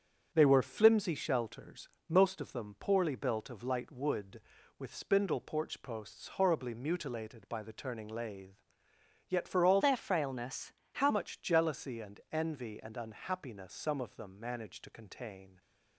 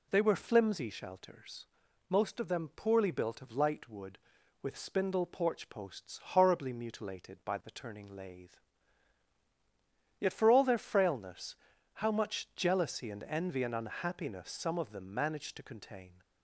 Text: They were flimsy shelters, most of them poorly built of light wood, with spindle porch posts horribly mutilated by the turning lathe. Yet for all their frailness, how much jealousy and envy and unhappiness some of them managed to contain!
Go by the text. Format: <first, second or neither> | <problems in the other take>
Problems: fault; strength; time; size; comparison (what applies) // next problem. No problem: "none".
second | starts louder than the rest; until 1.3 s; 7 dB // changes voice from "their" to "how"; from 9.8 to 11.1 s; 1.3 s long